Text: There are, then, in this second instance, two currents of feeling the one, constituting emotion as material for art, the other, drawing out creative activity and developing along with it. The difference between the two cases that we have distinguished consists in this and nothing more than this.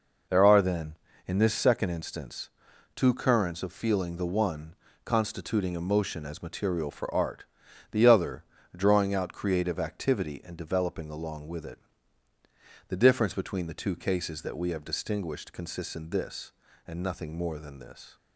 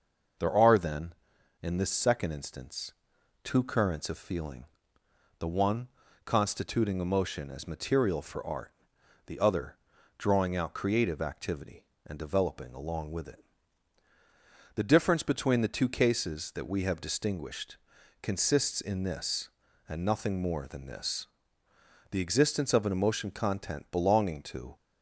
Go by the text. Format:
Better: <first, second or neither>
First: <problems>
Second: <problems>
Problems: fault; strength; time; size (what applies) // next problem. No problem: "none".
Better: first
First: none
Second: pauses between "feeling" and "the"; noticeable; at 4.6 s; 0.74 s long // pauses between "distinguished" and "consists"; noticeable; at 17.7 s; 0.46 s long // goes on to say "The existence of an emotion content belonging to"; strong; from 22.1 s on; 2.6 s long